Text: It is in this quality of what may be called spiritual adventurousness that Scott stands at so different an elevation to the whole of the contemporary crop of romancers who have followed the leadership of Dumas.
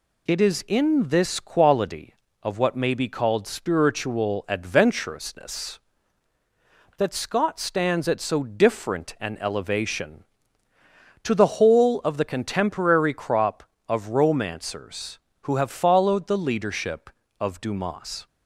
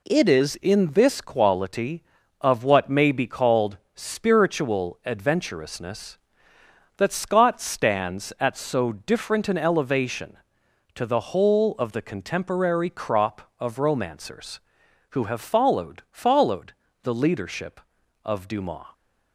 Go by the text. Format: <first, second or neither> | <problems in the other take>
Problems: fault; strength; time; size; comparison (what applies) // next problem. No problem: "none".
first | pauses between "called" and "spiritual"; slight; at 3.7 s; 0.18 s long // says "followed" twice; at 16.1 s